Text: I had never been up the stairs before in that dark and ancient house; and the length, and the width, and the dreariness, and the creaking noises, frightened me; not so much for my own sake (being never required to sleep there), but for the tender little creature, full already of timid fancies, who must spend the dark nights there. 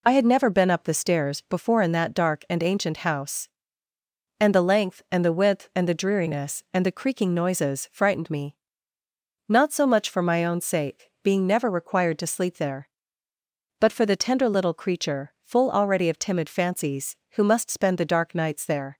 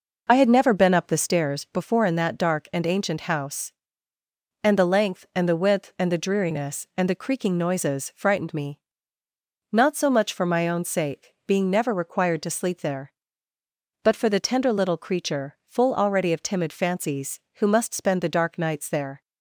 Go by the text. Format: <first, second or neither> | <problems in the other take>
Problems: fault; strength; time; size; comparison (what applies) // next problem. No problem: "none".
first | starts louder than the rest; noticeable; until 1.4 s; 5 dB